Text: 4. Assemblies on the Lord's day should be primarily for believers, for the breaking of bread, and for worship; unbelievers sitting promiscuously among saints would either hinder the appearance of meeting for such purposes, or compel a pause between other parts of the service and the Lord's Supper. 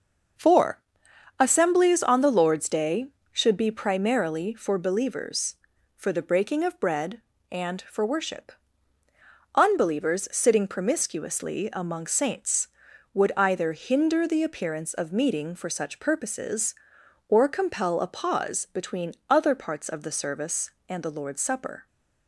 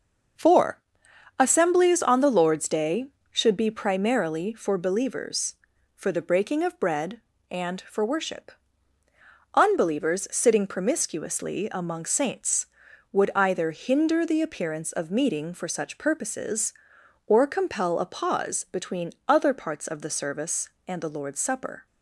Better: neither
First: pauses between "between" and "other"; slight; at 19.1 s; 0.16 s long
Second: pauses between "between" and "other"; slight; at 19.1 s; 0.16 s long

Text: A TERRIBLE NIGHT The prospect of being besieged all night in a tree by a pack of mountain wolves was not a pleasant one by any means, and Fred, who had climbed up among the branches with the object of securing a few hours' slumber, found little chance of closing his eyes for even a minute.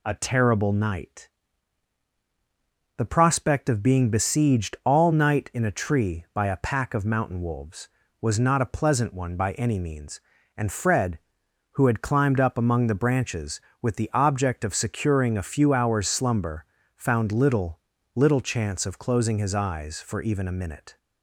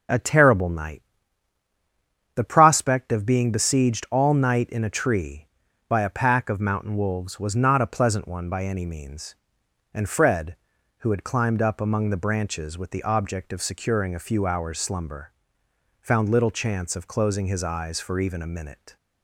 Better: second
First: pauses between "NIGHT" and "The"; strong; at 1.2 s; 1.6 s long // says "little" twice; at 18.1 s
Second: pauses between "NIGHT" and "The"; strong; at 1.0 s; 1.3 s long

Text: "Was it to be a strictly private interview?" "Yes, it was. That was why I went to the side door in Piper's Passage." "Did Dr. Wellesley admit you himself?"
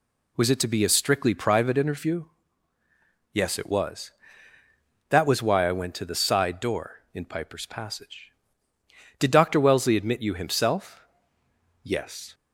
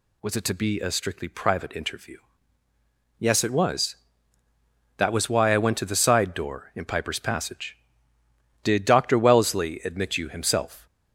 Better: second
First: goes on to say "Yes"; from 11.8 s on; 0.50 s long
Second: none

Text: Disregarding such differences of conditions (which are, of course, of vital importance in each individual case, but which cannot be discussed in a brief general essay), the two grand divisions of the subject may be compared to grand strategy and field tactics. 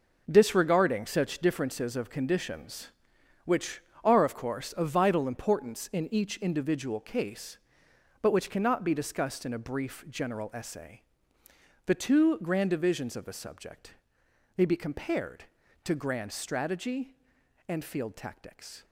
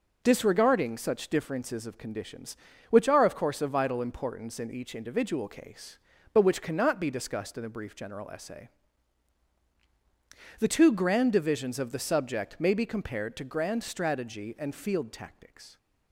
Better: second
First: gets quieter; strong; throughout; 9.5 dB // pauses between "subject" and "may"; noticeable; at 13.9 s; 0.62 s long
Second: none

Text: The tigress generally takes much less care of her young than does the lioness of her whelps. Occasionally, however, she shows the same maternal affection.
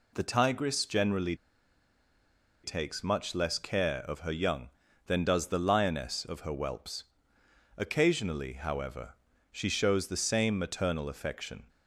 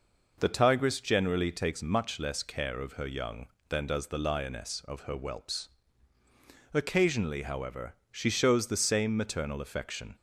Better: second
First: pauses between "generally" and "takes"; strong; at 1.3 s; 1.2 s long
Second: none

